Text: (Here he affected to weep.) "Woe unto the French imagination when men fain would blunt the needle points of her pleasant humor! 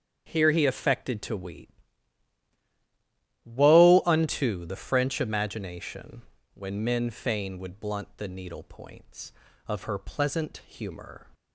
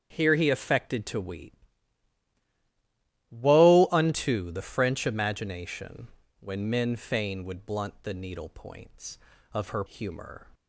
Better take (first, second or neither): first